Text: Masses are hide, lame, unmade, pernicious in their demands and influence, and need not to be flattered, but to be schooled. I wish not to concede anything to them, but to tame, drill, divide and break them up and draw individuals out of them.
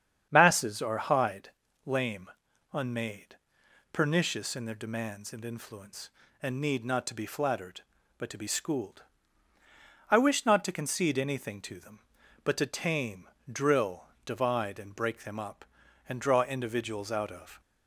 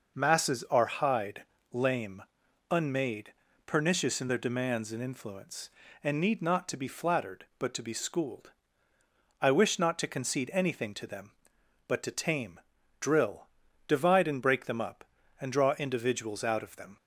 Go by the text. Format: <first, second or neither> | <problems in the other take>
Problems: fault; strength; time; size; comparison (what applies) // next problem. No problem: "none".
second | starts louder than the rest; strong; until 1.3 s; 8.5 dB // stops before "them"; at 17.6 s